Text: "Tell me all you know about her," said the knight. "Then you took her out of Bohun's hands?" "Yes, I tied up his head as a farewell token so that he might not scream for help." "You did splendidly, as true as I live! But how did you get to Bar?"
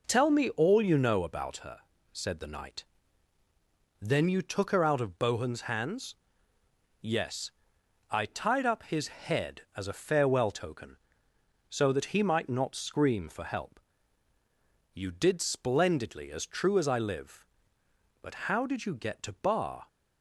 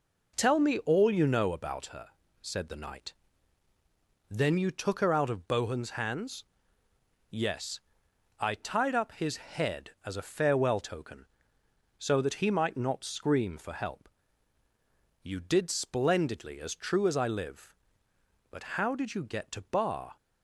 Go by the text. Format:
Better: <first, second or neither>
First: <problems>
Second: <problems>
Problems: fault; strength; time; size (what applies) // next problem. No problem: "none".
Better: neither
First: none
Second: none